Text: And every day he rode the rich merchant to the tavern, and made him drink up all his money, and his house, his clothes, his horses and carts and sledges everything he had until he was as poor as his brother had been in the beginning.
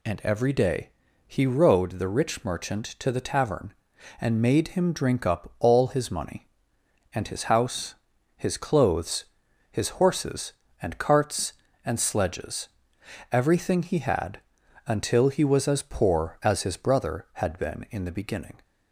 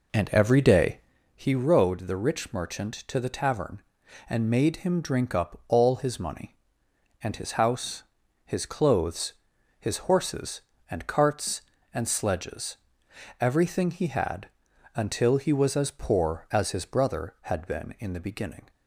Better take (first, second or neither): first